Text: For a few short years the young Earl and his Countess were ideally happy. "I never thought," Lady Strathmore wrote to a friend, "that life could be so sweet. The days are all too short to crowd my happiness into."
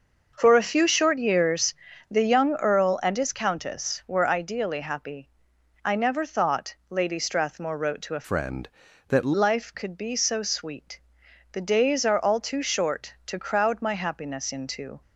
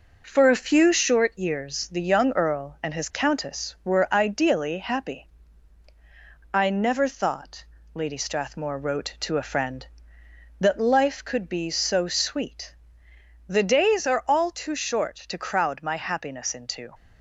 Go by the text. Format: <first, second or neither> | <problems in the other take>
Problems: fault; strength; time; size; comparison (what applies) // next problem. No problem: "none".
second | starts louder than the rest; noticeable; until 1.3 s; 6 dB // pauses between "years" and "the"; slight; at 1.7 s; 0.34 s long // changes voice from "friend" to "that"; from 8.2 to 9.3 s; 1.1 s long